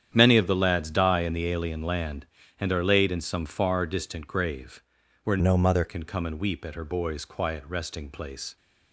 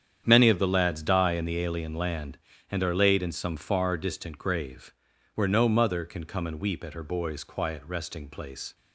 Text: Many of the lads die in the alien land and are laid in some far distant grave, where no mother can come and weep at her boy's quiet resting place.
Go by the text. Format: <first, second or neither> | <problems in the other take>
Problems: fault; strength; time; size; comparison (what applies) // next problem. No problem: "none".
second | starts louder than the rest; strong; until 1.1 s; 9 dB; strong in the second // changes voice from "no" to "mother"; from 5.3 to 5.8 s; 0.5 s long